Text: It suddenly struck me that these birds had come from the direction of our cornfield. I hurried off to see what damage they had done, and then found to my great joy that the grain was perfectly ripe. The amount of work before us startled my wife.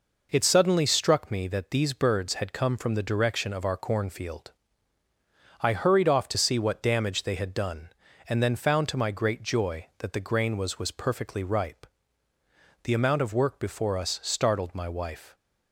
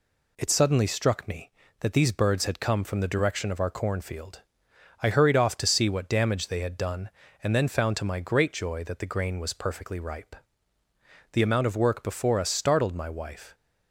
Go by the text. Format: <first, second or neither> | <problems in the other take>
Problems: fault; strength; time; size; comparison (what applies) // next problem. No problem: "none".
second | says "was" twice; at 10.7 s